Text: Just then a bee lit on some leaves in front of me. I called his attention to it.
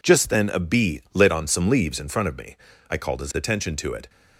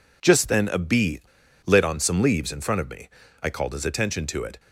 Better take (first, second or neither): first